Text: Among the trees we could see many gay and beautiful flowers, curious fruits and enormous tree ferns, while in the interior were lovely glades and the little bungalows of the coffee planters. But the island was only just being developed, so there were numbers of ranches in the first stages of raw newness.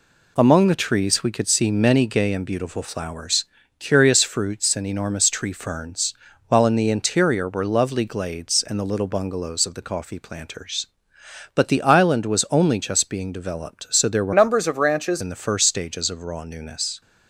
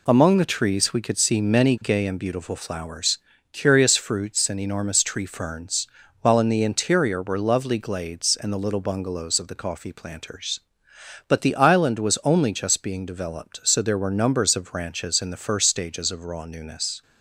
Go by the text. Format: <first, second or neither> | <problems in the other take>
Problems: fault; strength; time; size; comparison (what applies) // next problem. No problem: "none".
second | changes voice from "numbers" to "ranches"; from 14.3 to 15.2 s; 0.9 s long